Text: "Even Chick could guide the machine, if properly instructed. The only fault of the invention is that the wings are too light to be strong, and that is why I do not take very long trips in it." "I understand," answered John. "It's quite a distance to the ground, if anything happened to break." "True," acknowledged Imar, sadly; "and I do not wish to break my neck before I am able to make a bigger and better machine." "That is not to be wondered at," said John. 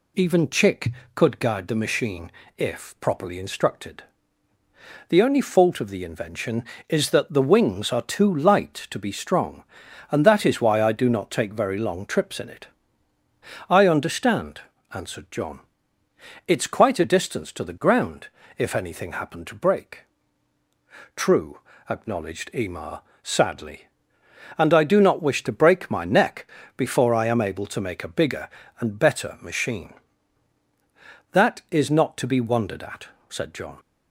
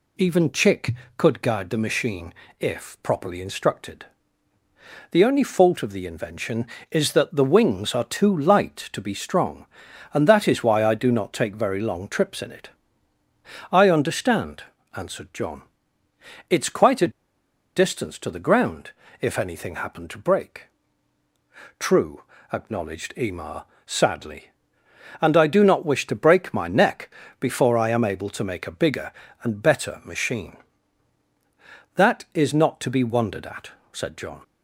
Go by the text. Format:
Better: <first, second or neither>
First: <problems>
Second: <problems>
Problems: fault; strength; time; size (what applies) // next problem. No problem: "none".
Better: first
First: pauses between "neck" and "before"; slight; at 26.4 s; 0.26 s long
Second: pauses between "a" and "distance"; noticeable; at 17.1 s; 0.64 s long // pauses between "neck" and "before"; slight; at 27.1 s; 0.26 s long